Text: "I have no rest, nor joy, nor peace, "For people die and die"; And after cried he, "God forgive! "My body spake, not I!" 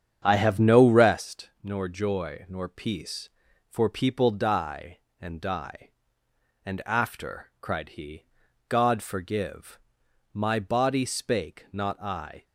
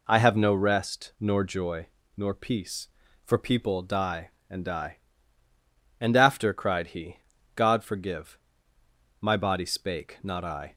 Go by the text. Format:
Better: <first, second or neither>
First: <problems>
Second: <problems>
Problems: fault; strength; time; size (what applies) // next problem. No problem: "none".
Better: second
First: starts louder than the rest; strong; until 1.2 s; 8.5 dB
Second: none